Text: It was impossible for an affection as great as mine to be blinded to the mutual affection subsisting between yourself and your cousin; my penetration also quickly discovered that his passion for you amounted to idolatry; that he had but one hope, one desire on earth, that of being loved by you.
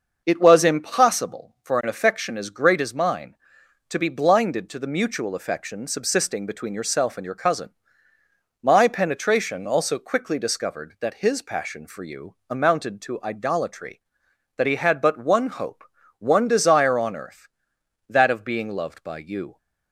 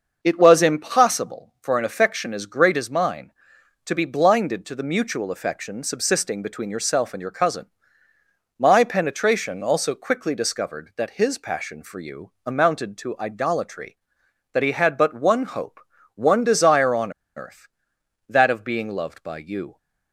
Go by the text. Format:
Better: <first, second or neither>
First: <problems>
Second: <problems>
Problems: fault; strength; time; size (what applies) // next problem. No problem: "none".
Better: first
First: starts louder than the rest; until 1.2 s; 6 dB // pauses between "you" and "amounted"; slight; at 12.3 s; 0.16 s long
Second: starts louder than the rest; until 1.2 s; 6 dB // pauses between "you" and "amounted"; slight; at 12.3 s; 0.16 s long // pauses between "on" and "earth"; slight; at 17.1 s; 0.25 s long